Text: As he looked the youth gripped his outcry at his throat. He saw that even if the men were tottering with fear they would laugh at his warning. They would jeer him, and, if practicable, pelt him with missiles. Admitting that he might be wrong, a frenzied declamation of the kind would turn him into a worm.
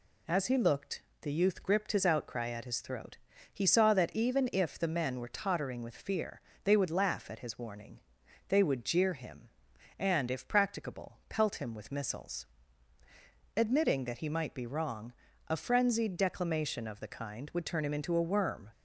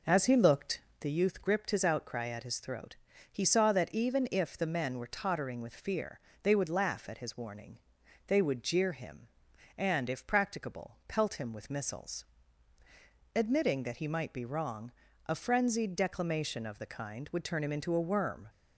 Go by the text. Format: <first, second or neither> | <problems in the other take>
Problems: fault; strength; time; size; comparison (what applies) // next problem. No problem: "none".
first | starts louder than the rest; noticeable; until 1.1 s; 4.5 dB // pauses between "looked" and "the"; slight; at 0.7 s; 0.20 s long; slight in the first // pauses between "fear" and "they"; slight; at 6.1 s; 0.24 s long; slight in the first